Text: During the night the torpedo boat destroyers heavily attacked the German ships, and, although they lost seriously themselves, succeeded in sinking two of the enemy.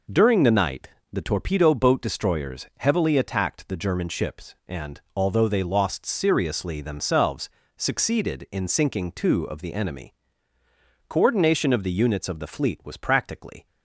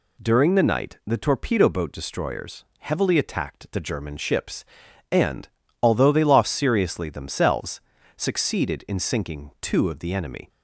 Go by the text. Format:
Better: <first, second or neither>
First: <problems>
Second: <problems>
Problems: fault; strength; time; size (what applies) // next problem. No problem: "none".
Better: second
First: pauses between "night" and "the"; slight; at 0.8 s; 0.22 s long // goes on to say "Coordination of the units of the fleet was practically"; strong; from 11.0 s on; 2.5 s long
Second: none